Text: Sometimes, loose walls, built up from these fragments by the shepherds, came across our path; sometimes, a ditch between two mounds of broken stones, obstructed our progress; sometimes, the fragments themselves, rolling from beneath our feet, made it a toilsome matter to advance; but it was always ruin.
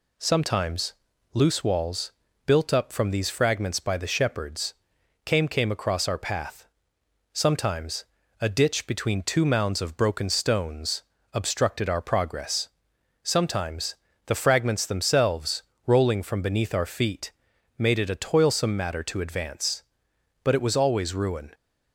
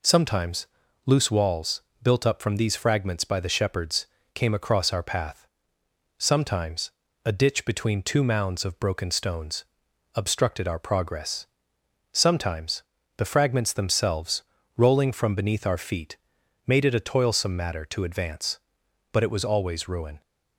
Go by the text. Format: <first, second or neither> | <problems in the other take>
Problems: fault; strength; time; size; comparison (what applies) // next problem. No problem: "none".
second | says "came" twice; at 5.4 s